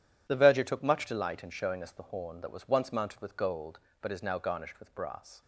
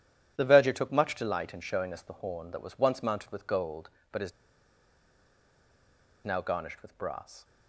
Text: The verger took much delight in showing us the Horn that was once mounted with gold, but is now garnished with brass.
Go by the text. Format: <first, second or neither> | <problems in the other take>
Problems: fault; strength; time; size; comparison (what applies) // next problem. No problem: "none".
first | pauses between "is" and "now"; strong; at 4.3 s; 1.9 s long